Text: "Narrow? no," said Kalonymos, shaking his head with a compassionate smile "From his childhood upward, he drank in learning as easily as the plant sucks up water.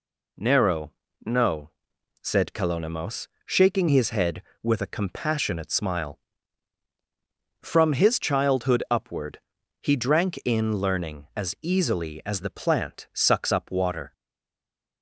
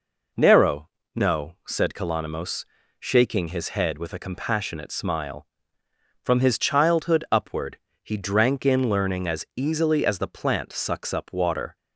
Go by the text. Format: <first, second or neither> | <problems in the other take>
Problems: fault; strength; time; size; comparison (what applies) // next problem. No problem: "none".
second | stays silent after the last word; slight; from 14.1 s on; 0.9 s long